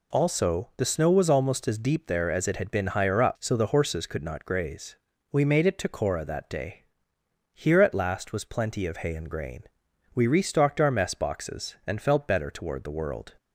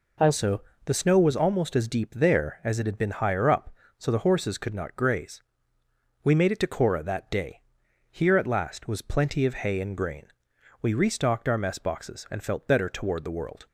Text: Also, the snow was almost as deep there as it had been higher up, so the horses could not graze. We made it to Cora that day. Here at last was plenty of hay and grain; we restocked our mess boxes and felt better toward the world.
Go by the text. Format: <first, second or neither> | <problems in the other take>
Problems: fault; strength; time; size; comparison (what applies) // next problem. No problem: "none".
neither | none